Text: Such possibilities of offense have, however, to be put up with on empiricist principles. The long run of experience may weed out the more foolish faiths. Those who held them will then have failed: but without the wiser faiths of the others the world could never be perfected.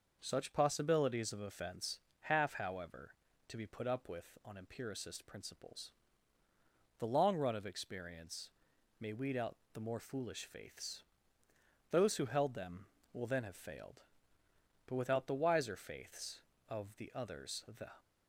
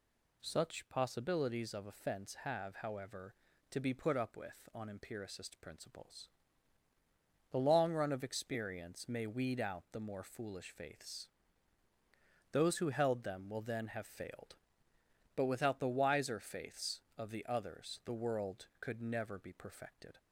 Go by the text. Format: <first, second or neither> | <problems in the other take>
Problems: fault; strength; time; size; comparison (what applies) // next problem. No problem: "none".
second | pauses between "experience" and "may"; noticeable; at 8.4 s; 0.50 s long // pauses between "out" and "the"; slight; at 9.5 s; 0.18 s long // stops before "world could never be perfected"; at 17.9 s